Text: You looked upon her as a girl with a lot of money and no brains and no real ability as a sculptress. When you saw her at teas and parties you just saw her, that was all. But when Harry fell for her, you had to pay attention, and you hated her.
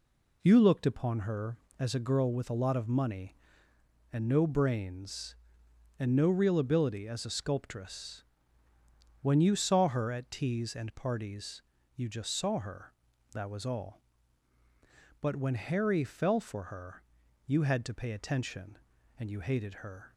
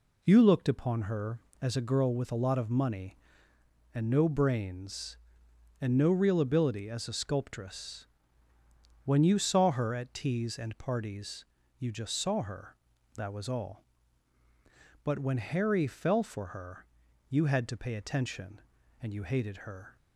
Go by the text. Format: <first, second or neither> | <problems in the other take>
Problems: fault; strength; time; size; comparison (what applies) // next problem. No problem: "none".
neither | pauses between "parties" and "you"; slight; the same in both